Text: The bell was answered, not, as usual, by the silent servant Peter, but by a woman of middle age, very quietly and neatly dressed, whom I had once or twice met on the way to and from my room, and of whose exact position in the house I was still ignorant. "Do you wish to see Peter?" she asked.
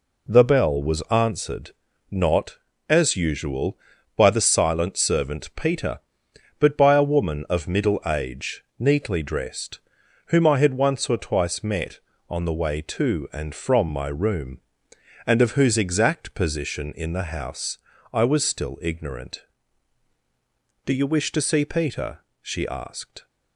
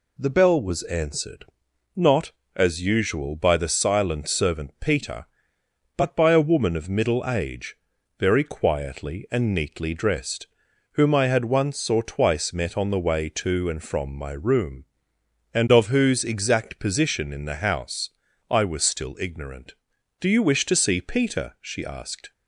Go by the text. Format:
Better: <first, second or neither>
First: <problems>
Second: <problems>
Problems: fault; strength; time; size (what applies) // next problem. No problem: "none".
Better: second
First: skips "very quietly and"; at 8.7 s // pauses between "house" and "I"; slight; at 17.7 s; 0.34 s long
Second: pauses between "house" and "I"; at 18.0 s; 0.40 s long